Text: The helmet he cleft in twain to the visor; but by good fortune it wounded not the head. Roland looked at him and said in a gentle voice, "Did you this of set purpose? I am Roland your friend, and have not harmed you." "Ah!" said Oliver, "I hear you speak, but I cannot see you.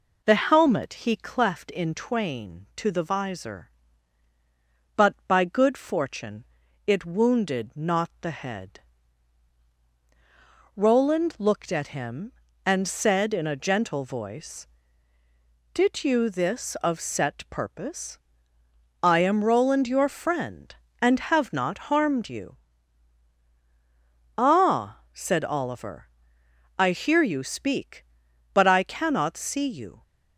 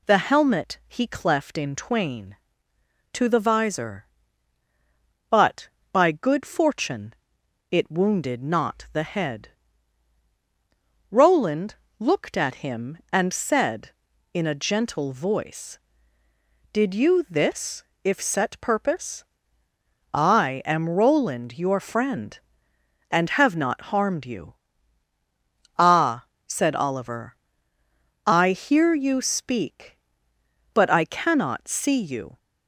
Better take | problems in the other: first | pauses between "fortune" and "it"; noticeable; at 7.1 s; 0.58 s long; also in the first // pauses between "Roland" and "looked"; slight; at 11.7 s; 0.24 s long // says "if" for "of"; at 18.0 s

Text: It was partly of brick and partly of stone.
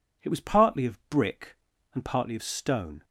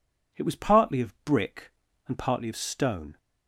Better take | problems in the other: neither | none

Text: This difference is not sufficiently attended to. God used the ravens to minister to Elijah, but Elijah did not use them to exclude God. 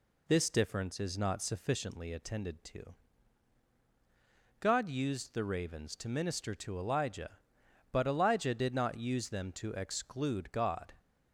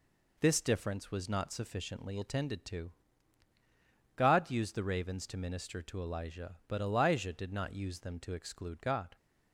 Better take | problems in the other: first | says "was" for "is"; at 1.0 s

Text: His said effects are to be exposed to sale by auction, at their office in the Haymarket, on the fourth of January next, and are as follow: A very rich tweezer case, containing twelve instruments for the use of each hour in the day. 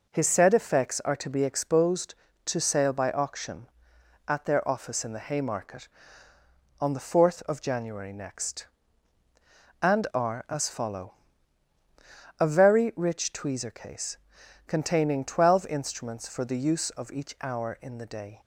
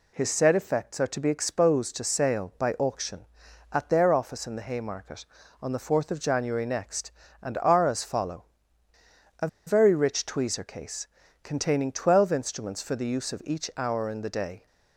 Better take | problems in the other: first | pauses between "A" and "very"; slight; at 9.4 s; 0.19 s long

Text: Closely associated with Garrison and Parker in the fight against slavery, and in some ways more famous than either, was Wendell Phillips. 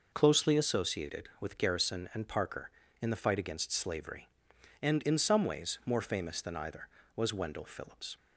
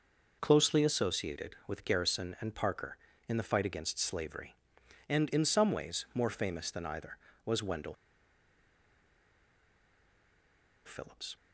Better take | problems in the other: first | pauses between "Wendell" and "Phillips"; strong; at 7.9 s; 2.9 s long

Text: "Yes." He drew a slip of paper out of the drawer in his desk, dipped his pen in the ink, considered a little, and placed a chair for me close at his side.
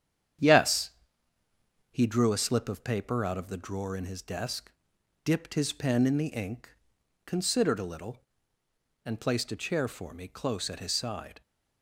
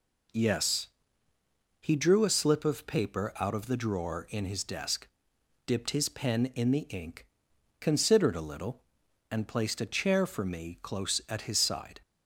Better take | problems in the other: second | gets quieter; throughout; 6.5 dB

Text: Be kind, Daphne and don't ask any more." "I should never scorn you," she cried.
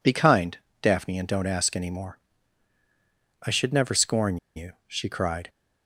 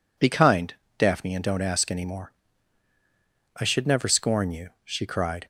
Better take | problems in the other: second | pauses between "scorn" and "you"; slight; at 4.3 s; 0.19 s long

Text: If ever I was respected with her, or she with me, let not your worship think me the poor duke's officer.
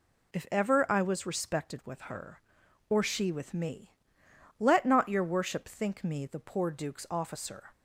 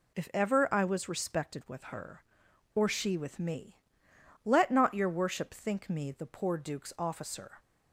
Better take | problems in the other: neither | none

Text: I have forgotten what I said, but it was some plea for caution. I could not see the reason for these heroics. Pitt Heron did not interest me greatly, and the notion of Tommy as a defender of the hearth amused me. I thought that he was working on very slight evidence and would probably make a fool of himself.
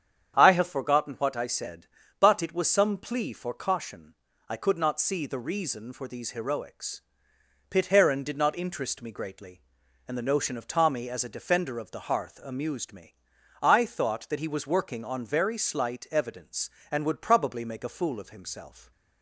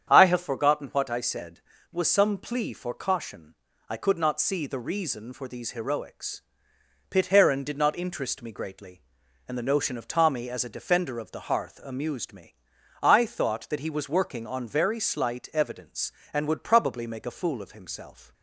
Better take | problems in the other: first | starts louder than the rest; strong; until 1.1 s; 8.5 dB; strong in the first // skips "but it"; at 1.7 s

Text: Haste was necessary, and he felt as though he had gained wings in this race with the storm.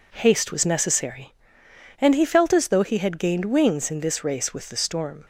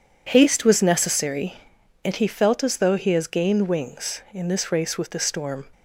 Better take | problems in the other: first | says "has" for "had"; at 3.1 s

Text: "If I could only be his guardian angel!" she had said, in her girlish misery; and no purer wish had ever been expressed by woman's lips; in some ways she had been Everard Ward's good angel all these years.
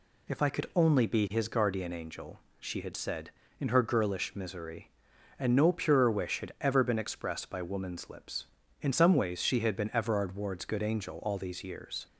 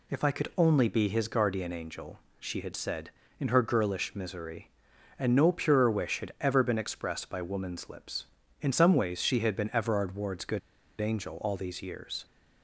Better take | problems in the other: first | pauses between "good" and "angel"; at 10.5 s; 0.41 s long

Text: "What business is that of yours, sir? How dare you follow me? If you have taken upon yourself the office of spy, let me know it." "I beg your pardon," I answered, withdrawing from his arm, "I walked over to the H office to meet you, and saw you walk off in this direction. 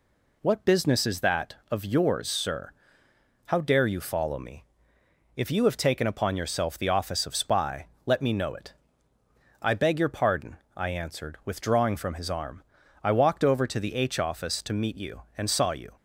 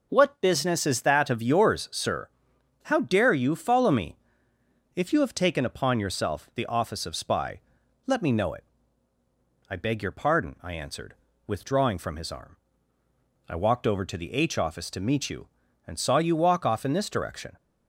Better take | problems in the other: second | stops before "walk off in this direction"; at 15.9 s

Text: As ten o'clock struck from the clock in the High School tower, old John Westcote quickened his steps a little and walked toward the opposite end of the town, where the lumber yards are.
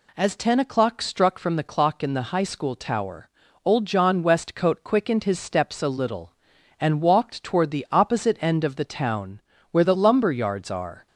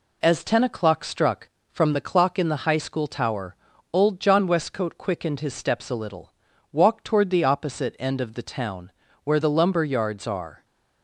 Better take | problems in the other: first | skips "and"; at 6.5 s

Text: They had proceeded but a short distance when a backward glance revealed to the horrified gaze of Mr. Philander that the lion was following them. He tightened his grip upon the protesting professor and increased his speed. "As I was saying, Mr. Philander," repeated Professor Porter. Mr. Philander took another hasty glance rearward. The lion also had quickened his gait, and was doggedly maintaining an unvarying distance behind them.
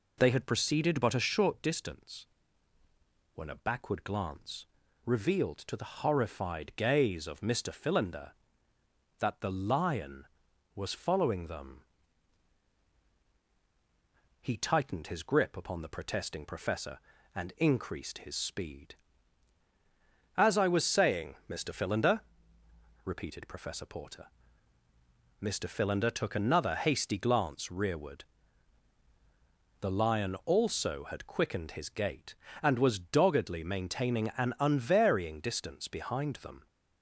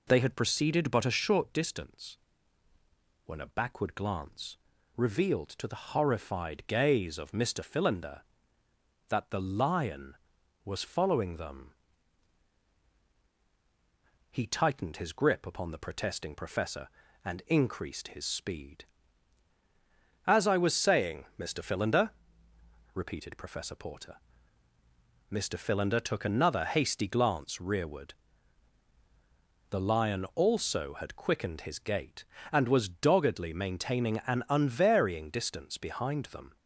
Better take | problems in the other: neither | pauses between "distance" and "when"; the same in both // pauses between "glance" and "revealed"; the same in both

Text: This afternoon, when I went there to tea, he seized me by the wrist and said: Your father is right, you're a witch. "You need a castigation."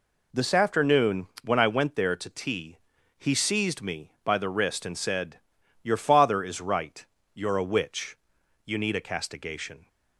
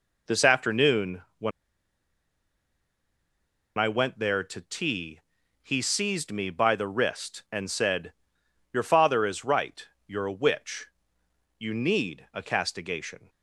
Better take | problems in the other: first | pauses between "when" and "I"; strong; at 1.5 s; 2.2 s long

